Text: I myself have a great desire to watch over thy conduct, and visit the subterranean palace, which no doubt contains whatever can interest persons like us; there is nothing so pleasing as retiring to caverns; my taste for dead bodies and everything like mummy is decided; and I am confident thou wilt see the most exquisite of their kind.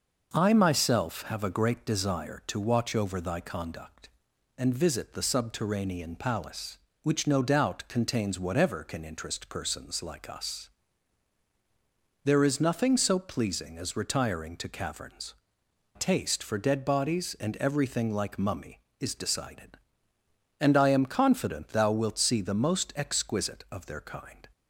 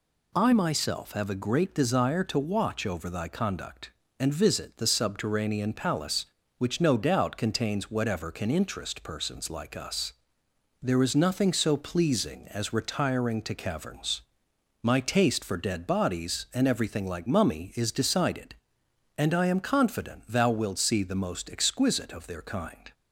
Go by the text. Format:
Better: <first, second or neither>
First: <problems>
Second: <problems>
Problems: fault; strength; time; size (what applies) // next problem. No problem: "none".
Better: second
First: starts louder than the rest; noticeable; until 1.3 s; 6 dB // skips "my"; at 15.6 s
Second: none